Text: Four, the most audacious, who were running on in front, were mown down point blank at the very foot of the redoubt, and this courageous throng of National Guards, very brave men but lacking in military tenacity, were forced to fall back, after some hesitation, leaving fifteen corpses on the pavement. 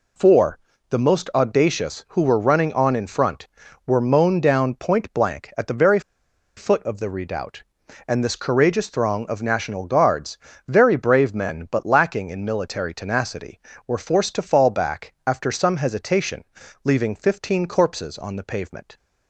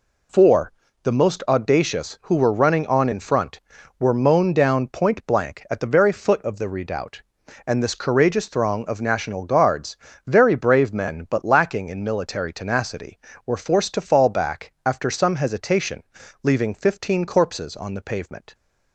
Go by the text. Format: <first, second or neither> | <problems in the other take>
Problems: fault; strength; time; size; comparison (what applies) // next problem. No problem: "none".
second | pauses between "very" and "foot"; noticeable; at 5.9 s; 0.56 s long